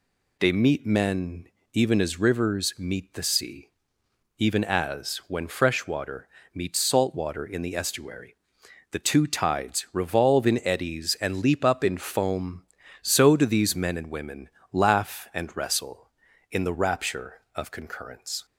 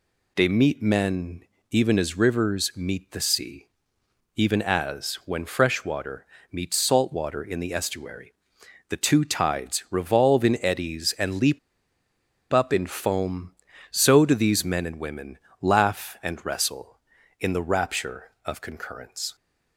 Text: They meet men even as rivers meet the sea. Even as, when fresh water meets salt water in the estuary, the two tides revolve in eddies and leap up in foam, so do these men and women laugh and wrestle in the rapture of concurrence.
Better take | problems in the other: first | pauses between "men" and "even"; slight; at 1.4 s; 0.28 s long; slight in the first // pauses between "water" and "meets"; slight; at 6.2 s; 0.24 s long; slight in the first // pauses between "leap" and "up"; noticeable; at 11.5 s; 0.93 s long // pauses between "women" and "laugh"; slight; at 15.3 s; 0.22 s long; slight in the first

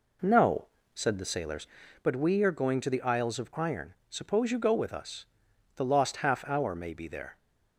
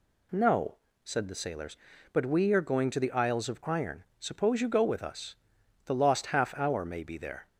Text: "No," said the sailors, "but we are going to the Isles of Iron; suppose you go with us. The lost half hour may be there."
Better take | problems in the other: second | starts louder than the rest; until 2.1 s; 3.5 dB

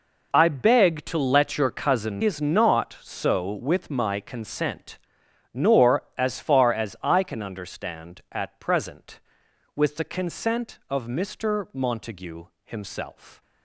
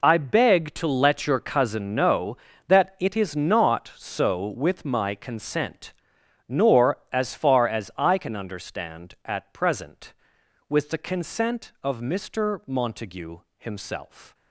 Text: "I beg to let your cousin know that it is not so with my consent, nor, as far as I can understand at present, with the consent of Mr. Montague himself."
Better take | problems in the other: second | skips "know that it"; at 2.2 s // pauses between "Montague" and "himself"; slight; at 12.4 s; 0.18 s long; slight in the second

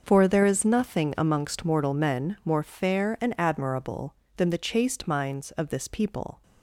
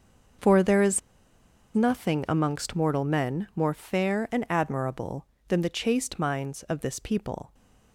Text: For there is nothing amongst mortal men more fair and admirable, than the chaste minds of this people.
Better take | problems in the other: first | starts louder than the rest; until 2.1 s; 6 dB; also in the first // pauses between "is" and "nothing"; noticeable; at 1.0 s; 0.75 s long

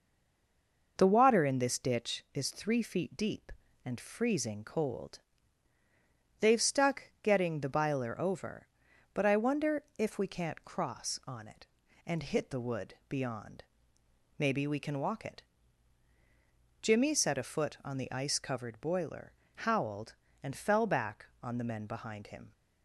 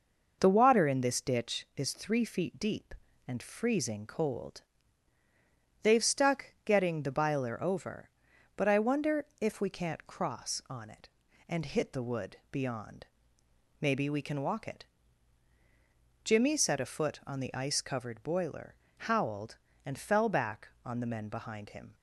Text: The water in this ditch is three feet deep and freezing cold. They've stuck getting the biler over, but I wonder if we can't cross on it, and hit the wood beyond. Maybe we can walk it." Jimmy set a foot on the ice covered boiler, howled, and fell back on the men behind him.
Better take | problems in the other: second | stays silent before the first word; until 0.9 s; 0.9 s long

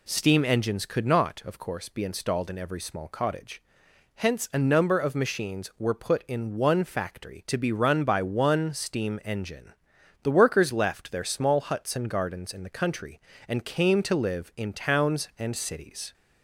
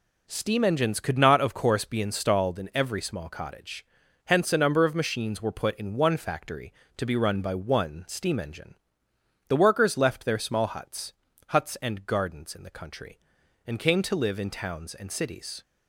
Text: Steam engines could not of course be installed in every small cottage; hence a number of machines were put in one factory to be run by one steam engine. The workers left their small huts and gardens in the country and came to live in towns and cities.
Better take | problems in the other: first | says "huts" twice; at 11.5 s

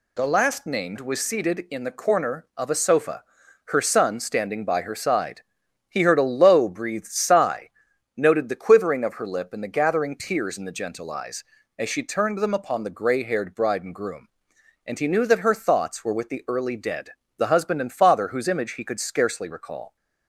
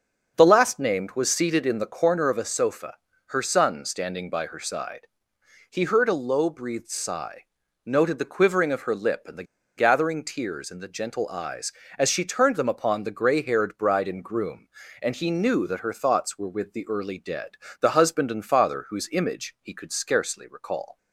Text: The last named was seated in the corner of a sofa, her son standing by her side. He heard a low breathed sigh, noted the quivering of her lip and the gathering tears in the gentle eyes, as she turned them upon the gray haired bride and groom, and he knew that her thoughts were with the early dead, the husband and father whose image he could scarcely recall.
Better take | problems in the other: first | starts louder than the rest; until 1.3 s; 6 dB // pauses between "the" and "gathering"; slight; at 9.4 s; 0.33 s long

